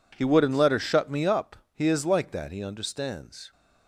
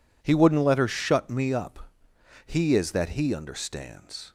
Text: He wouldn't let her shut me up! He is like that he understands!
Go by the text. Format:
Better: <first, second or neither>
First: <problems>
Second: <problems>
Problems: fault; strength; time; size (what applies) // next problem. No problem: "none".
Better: first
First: none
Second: skips "like"; at 2.9 s